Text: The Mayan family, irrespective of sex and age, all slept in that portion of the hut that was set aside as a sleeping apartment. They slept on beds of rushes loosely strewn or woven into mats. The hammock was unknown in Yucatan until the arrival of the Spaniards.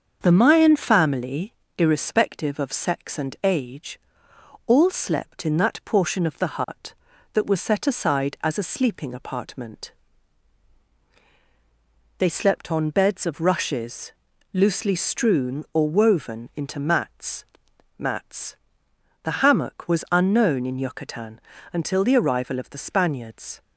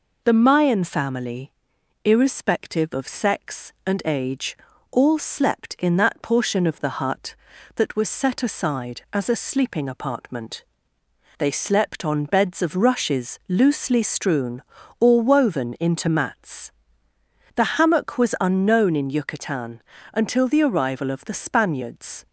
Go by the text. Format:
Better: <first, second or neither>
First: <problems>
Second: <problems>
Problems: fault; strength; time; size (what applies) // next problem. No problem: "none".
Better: second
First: starts louder than the rest; until 1.2 s; 7 dB // pauses between "rushes" and "loosely"; at 14.1 s; 0.38 s long // says "mats" twice; at 17.9 s // pauses between "Yucatan" and "until"; slight; at 21.3 s; 0.32 s long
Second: pauses between "Yucatan" and "until"; slight; at 19.7 s; 0.32 s long